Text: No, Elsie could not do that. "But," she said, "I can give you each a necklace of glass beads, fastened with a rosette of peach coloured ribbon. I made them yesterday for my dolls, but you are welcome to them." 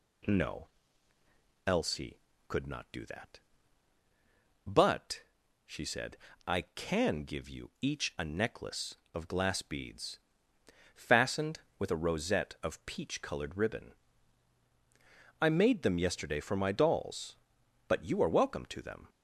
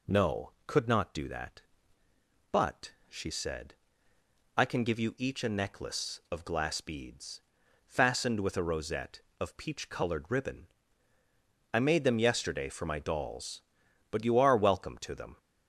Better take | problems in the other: first | skips "Elsie"; at 0.5 s

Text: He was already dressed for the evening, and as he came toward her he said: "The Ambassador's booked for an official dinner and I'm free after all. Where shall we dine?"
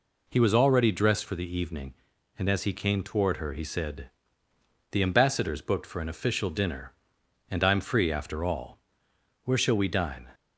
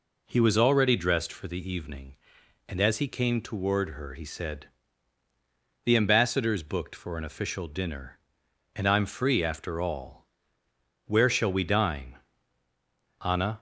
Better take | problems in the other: first | goes on to say "Anna"; slight; from 13.2 s on; 0.36 s long

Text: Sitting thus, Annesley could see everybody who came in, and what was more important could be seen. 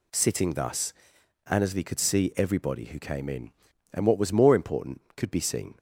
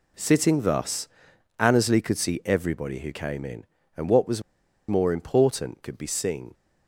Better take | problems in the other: first | pauses between "was" and "more"; noticeable; at 4.4 s; 0.47 s long

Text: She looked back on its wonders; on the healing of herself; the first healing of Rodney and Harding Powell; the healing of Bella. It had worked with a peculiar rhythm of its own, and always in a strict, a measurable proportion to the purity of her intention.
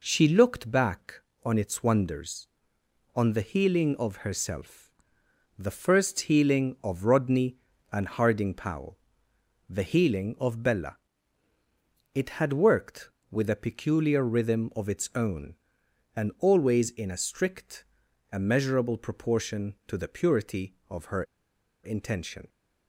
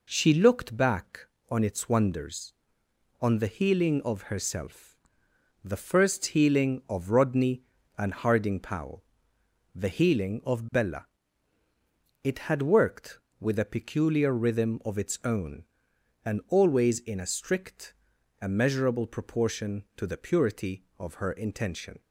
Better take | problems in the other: second | pauses between "her" and "intention"; noticeable; at 21.2 s; 0.60 s long

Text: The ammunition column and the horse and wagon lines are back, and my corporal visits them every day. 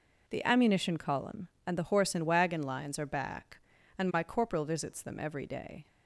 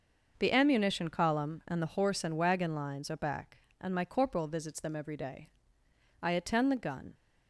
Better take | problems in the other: first | starts louder than the rest; noticeable; until 1.3 s; 6 dB // goes on to say "I attend the gun"; noticeable; from 6.2 s on; 0.92 s long

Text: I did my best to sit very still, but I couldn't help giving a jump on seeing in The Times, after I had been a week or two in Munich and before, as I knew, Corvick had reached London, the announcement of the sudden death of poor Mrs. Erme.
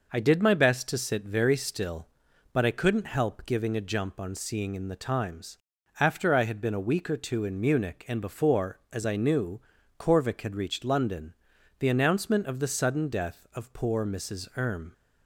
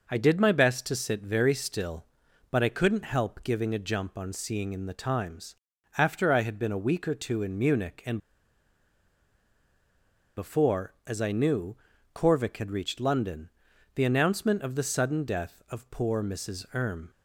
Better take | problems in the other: first | pauses between "and" and "before"; strong; at 8.1 s; 2.1 s long

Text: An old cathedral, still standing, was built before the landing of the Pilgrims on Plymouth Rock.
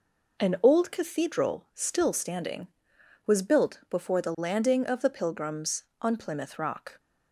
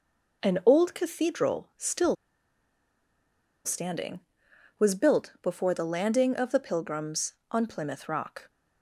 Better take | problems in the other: first | pauses between "still" and "standing"; strong; at 2.1 s; 1.5 s long

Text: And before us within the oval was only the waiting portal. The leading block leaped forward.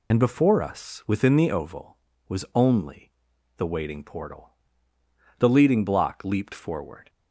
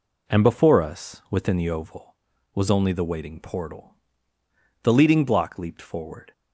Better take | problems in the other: second | loses the start of "And"; at 0.1 s; 60 ms // pauses between "only" and "the"; noticeable; at 3.1 s; 0.46 s long

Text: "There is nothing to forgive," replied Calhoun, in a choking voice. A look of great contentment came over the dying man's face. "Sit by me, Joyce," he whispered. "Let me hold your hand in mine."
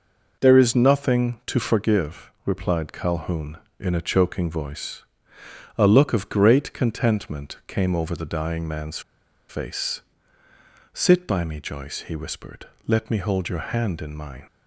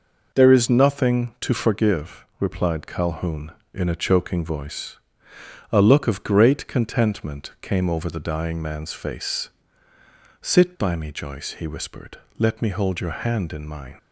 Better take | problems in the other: second | pauses between "man's" and "face"; noticeable; at 8.9 s; 0.49 s long

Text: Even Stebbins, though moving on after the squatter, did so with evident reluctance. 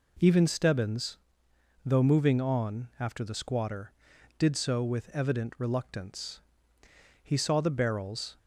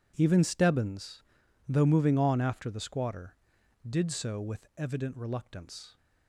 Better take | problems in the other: second | goes on to say "He saw the barrels"; noticeable; from 7.2 s on; 1.1 s long

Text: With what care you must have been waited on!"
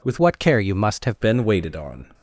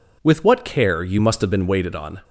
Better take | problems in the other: second | changes voice from "what" to "have"; from 0.1 to 1.1 s; 1.0 s long

